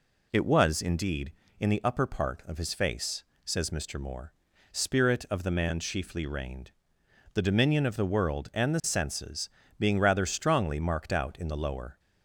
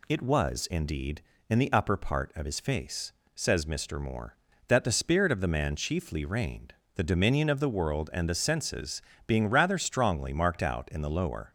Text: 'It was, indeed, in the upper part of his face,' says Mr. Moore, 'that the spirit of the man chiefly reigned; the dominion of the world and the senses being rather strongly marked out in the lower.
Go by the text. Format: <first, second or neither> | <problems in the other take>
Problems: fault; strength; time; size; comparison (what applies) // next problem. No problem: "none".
second | skips "that the"; at 4.5 s // pauses between "senses" and "being"; slight; at 9.4 s; 0.28 s long; slight in the second